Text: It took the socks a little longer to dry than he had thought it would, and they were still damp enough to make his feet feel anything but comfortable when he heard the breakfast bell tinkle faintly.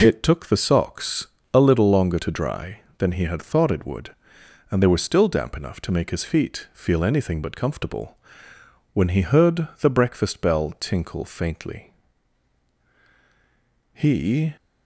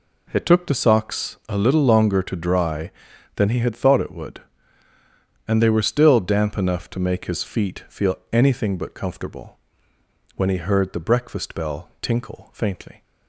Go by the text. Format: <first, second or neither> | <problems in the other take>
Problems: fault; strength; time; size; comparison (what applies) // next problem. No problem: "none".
second | pauses between "socks" and "a"; slight; at 1.2 s; 0.26 s long // pauses between "comfortable" and "when"; noticeable; at 8.1 s; 0.78 s long; noticeable in the second // goes on to say "He"; noticeable; from 13.9 s on; 0.62 s long